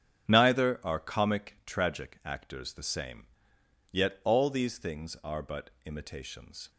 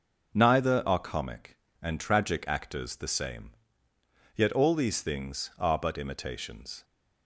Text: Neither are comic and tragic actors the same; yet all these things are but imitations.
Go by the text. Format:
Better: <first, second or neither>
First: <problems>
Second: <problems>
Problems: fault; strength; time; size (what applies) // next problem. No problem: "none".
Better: second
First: starts louder than the rest; strong; until 1.3 s; 8.5 dB // skips "and"; at 1.6 s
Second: starts louder than the rest; until 1.3 s; 6 dB